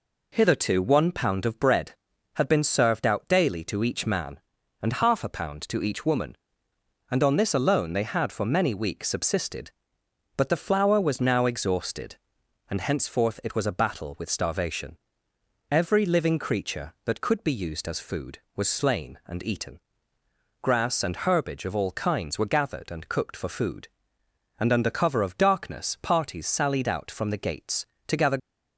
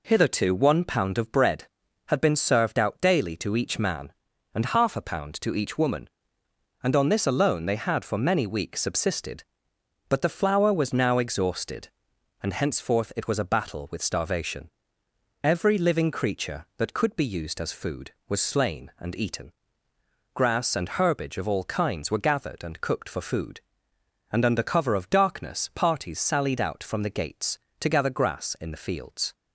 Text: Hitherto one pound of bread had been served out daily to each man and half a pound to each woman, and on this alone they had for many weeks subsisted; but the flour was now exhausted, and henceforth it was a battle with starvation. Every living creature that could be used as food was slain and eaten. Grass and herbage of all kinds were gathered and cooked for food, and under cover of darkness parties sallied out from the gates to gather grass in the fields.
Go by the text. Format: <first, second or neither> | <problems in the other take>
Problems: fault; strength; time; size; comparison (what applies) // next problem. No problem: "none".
second | stops before "grass in the fields"; at 28.3 s